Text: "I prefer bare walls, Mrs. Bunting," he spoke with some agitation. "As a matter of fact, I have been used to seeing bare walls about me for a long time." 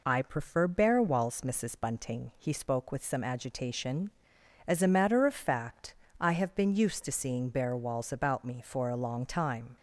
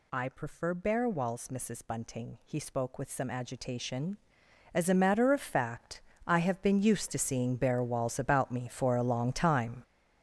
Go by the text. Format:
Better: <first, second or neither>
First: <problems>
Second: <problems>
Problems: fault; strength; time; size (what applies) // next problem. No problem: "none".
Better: first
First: none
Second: gets louder; strong; throughout; 10 dB